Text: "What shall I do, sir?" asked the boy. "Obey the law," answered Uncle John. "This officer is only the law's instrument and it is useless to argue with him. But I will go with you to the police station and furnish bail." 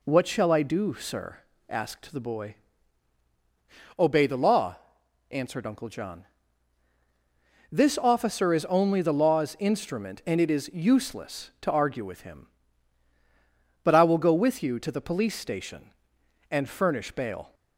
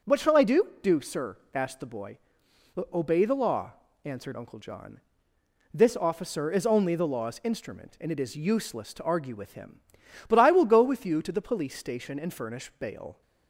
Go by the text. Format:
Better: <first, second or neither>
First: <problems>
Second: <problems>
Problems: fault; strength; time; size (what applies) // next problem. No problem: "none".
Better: first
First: none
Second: says "do" twice; at 0.8 s